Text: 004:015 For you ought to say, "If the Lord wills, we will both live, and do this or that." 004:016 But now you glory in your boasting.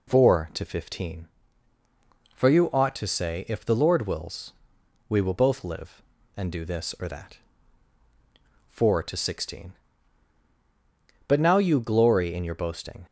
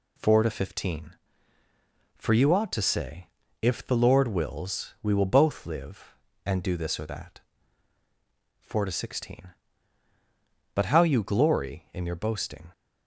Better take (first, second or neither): first